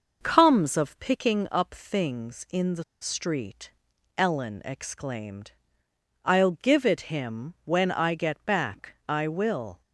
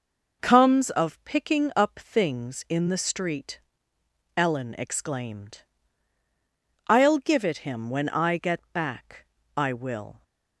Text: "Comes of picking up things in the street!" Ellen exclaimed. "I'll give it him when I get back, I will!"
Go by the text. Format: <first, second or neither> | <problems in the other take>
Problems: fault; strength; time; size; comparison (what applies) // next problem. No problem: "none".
second | pauses between "the" and "street"; slight; at 2.8 s; 0.17 s long